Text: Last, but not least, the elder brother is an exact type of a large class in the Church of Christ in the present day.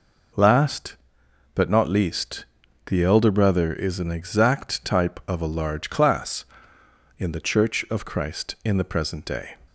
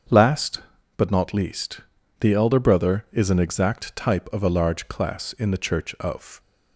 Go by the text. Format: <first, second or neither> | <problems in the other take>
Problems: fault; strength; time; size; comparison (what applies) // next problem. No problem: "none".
first | starts louder than the rest; until 1.4 s; 7 dB // stops before "Christ in the present day"; at 6.3 s